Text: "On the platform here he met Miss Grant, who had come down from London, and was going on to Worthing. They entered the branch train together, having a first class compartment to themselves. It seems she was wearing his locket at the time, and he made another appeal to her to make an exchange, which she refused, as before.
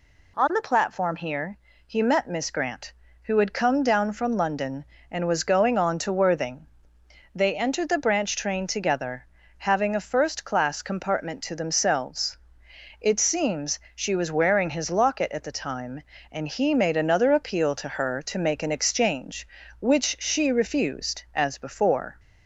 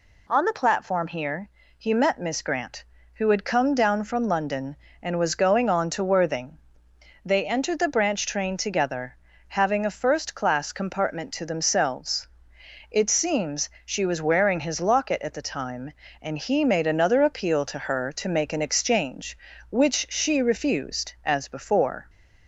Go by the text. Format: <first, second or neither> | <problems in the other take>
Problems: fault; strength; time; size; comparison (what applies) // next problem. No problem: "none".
neither | pauses between "here" and "he"; slight; the same in both // pauses between "seems" and "she"; slight; the same in both